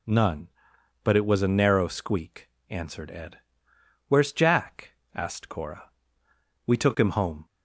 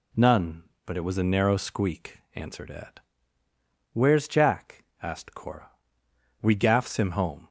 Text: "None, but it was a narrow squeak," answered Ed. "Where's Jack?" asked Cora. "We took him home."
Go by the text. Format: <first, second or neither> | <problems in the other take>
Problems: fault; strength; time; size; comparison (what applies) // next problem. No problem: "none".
first | says "gaffs" for "took"; at 6.5 s